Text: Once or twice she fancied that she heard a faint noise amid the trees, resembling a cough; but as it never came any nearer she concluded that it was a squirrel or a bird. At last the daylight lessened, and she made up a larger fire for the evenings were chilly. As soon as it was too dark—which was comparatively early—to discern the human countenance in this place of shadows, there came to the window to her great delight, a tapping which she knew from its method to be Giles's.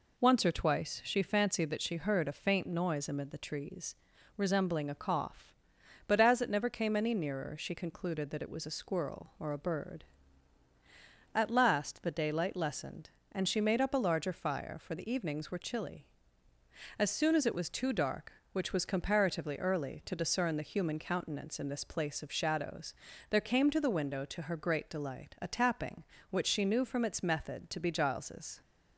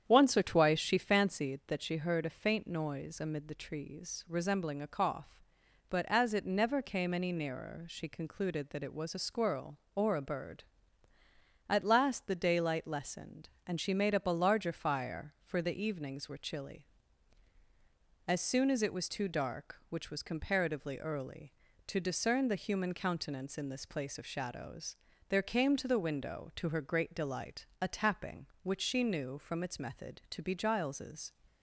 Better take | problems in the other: first | starts louder than the rest; strong; until 1.5 s; 8.5 dB

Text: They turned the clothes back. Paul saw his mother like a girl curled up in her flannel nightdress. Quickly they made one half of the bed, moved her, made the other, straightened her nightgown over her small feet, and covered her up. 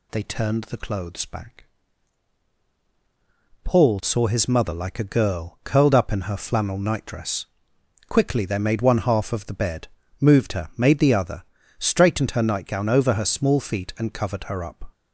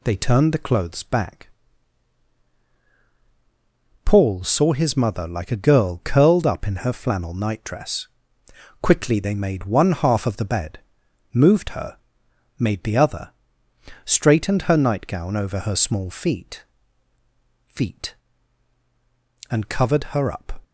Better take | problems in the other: first | says "feet" twice; at 17.6 s

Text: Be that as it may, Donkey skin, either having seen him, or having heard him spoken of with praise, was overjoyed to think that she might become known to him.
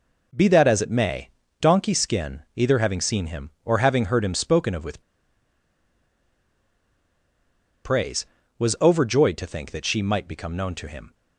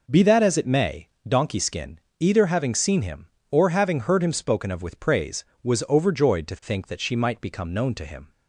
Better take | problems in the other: second | pauses between "with" and "praise"; strong; at 5.0 s; 2.8 s long

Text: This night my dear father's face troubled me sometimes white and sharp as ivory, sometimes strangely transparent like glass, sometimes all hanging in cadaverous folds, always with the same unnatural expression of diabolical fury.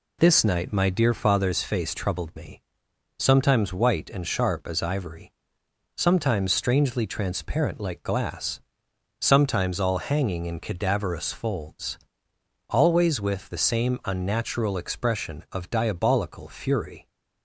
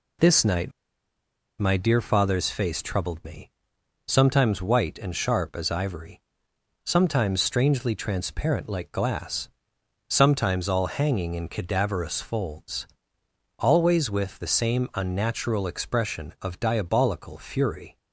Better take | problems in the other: first | pauses between "night" and "my"; noticeable; at 0.6 s; 0.88 s long // pauses between "me" and "sometimes"; noticeable; at 3.4 s; 0.60 s long; noticeable in the first

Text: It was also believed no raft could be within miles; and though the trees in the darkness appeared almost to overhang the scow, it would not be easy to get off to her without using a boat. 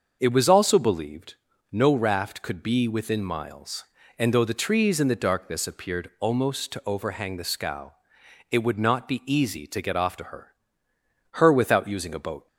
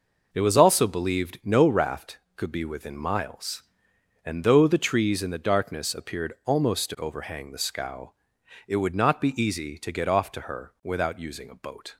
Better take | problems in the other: second | starts louder than the rest; until 1.2 s; 6.5 dB // pauses between "believed" and "no"; at 1.3 s; 0.38 s long // says "her" twice; at 11.3 s

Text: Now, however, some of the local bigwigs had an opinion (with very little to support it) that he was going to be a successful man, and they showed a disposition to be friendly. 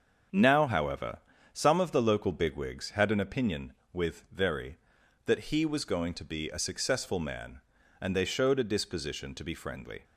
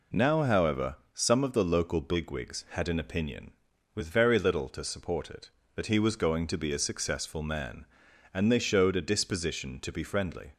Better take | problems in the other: second | starts louder than the rest; until 1.6 s; 6.5 dB // skips "little to support it"; at 4.9 s

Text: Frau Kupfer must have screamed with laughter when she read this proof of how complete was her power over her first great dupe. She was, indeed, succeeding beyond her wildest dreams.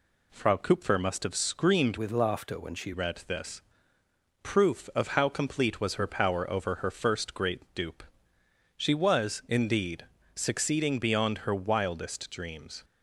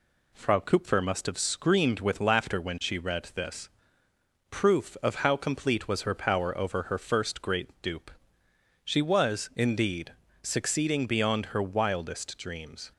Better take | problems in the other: second | changes voice from "with" to "she"; from 1.9 to 2.9 s; 1.0 s long // pauses between "this" and "proof"; noticeable; at 3.6 s; 0.80 s long; noticeable in the second

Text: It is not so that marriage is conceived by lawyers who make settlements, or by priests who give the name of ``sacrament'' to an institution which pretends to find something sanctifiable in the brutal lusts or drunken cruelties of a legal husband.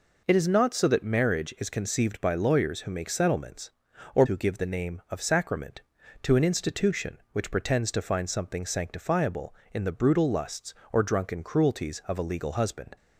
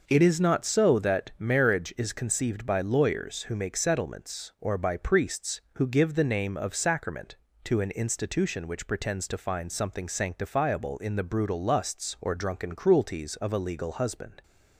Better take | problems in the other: second | skips "by priests"; at 4.2 s

